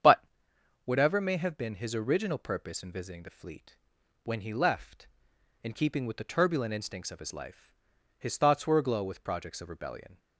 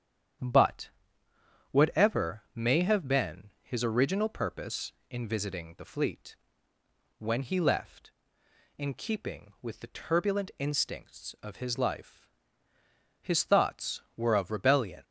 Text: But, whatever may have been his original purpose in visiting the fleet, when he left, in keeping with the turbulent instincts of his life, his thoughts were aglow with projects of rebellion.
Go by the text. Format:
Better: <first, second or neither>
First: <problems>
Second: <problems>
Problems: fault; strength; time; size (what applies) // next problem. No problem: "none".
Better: first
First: starts louder than the rest; strong; until 1.6 s; 8 dB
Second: starts louder than the rest; strong; until 2.2 s; 9 dB // skips "aglow with projects"; at 14.3 s